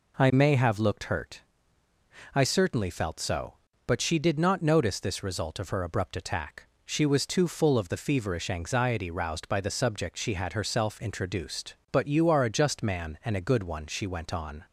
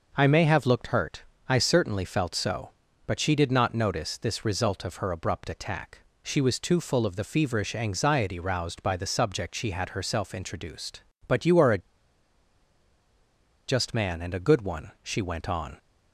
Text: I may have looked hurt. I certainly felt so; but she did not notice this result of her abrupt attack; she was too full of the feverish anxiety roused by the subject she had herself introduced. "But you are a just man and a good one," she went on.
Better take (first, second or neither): first